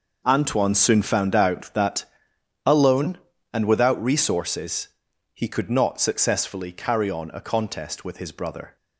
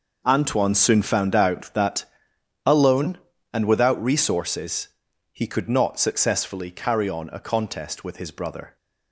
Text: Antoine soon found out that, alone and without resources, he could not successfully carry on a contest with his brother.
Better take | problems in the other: neither | none

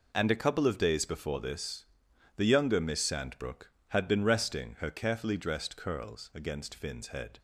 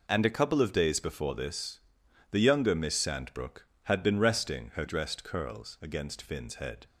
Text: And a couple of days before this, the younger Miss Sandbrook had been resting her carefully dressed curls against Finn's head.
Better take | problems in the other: first | skips "carefully"; at 4.8 s

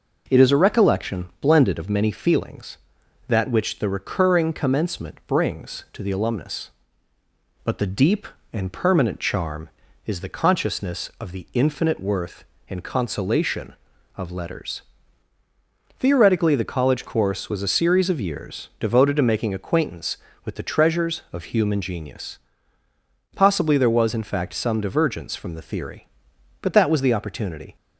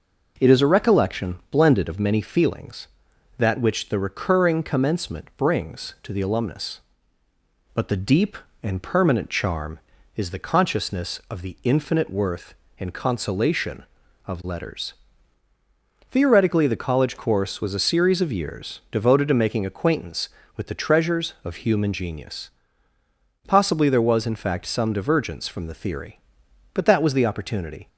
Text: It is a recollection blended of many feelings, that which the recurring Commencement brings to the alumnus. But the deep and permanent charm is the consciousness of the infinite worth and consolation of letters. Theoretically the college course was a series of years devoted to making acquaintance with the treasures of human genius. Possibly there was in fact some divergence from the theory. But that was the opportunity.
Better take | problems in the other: neither | none

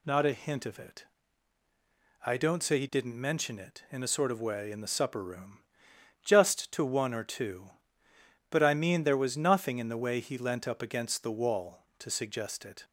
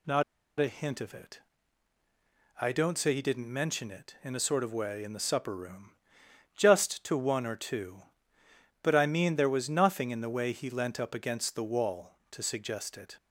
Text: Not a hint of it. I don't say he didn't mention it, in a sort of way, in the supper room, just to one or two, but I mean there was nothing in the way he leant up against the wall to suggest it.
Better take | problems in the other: first | pauses between "Not" and "a"; at 0.2 s; 0.37 s long

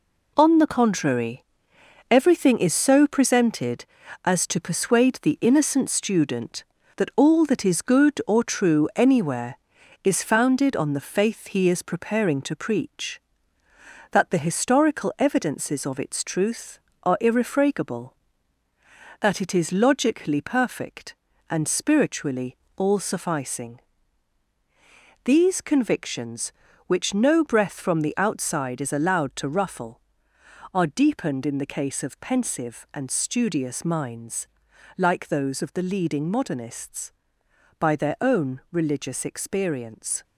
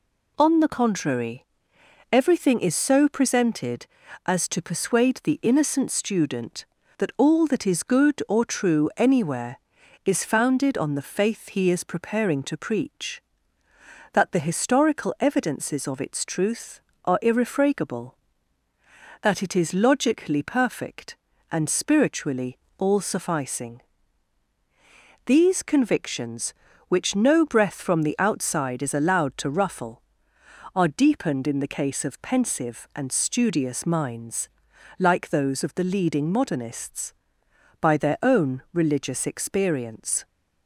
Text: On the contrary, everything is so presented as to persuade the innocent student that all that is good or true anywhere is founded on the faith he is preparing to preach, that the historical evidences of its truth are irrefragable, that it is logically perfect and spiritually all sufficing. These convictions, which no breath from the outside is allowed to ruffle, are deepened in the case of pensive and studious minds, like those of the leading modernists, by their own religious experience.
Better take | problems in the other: second | gets quieter; throughout; 7 dB // pauses between "spiritually" and "all"; slight; at 22.5 s; 0.18 s long; slight in the second

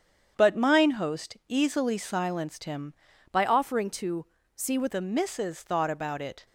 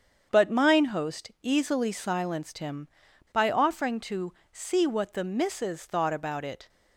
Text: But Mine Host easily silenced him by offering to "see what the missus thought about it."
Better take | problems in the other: second | starts louder than the rest; strong; until 1.3 s; 8 dB; strong in the second // changes voice from "by" to "what"; from 3.3 to 4.9 s; 1.6 s long // pauses between "to" and "see"; slight; at 4.2 s; 0.32 s long; slight in the second

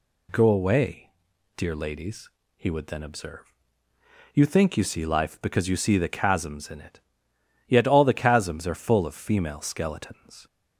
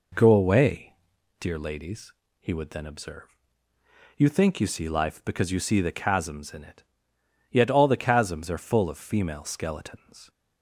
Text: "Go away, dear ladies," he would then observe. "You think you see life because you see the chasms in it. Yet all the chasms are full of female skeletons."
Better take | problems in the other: first | starts louder than the rest; noticeable; until 1.3 s; 4 dB

